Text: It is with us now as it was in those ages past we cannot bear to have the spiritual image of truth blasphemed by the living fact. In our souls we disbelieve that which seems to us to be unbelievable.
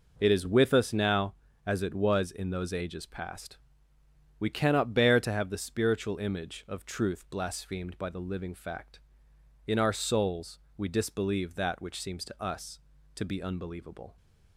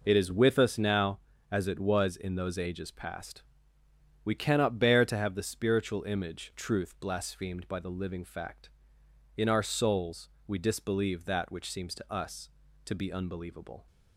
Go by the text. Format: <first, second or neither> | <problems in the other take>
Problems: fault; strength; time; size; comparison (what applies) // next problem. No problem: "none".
first | pauses between "past" and "we"; noticeable; at 3.4 s; 0.80 s long; noticeable in the first // skips "of"; at 6.5 s // pauses between "souls" and "we"; slight; at 10.2 s; 0.18 s long; slight in the first